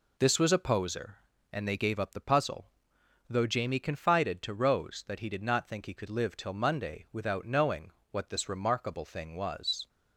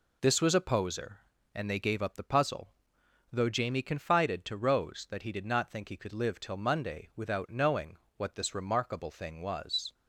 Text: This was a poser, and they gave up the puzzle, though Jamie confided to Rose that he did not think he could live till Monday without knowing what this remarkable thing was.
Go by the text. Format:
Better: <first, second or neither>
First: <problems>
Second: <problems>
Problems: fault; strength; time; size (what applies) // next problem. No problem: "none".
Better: neither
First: pauses between "knowing" and "what"; slight; at 7.8 s; 0.22 s long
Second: pauses between "knowing" and "what"; slight; at 7.9 s; 0.22 s long